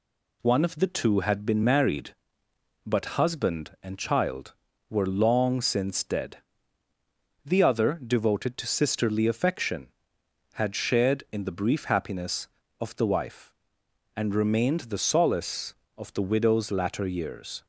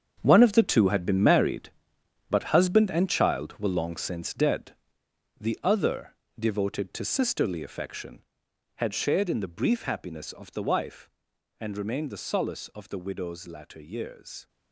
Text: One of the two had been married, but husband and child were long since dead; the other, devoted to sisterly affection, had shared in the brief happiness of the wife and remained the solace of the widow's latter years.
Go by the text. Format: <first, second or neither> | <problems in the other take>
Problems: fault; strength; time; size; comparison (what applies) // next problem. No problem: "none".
first | gets quieter; strong; throughout; 11.5 dB